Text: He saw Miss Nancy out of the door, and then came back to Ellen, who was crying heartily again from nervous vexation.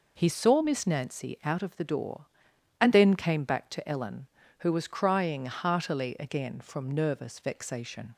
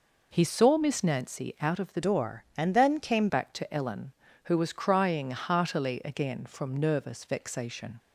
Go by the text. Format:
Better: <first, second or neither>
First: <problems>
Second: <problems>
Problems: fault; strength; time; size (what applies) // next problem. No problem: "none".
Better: first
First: none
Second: changes voice from "door" to "came"; from 2.0 to 3.2 s; 1.2 s long